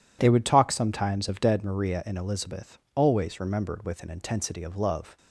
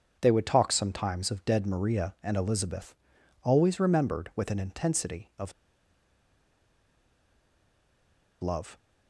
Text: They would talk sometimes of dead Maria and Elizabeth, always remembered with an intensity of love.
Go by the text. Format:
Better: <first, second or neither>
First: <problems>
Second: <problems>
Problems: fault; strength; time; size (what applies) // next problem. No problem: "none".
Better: first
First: none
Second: pauses between "of" and "love"; strong; at 5.5 s; 2.9 s long